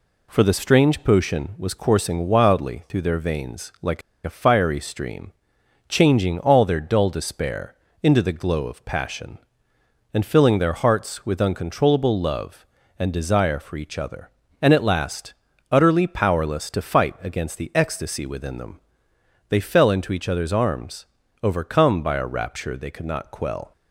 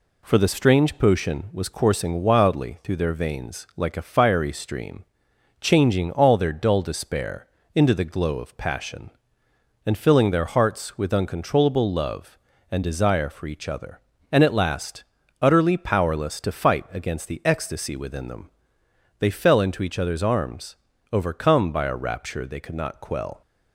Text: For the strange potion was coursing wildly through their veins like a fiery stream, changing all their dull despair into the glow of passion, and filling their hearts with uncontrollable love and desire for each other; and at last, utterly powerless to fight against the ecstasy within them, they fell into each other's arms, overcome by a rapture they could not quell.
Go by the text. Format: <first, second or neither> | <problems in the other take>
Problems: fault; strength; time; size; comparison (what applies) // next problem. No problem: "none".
second | pauses between "like" and "a"; slight; at 4.0 s; 0.24 s long // pauses between "despair" and "into"; slight; at 7.7 s; 0.28 s long; slight in the second